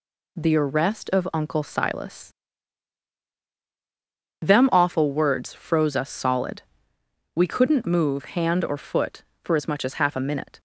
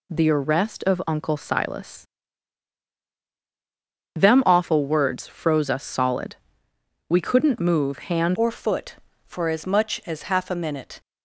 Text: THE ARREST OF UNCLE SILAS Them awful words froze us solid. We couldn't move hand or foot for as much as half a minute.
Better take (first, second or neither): first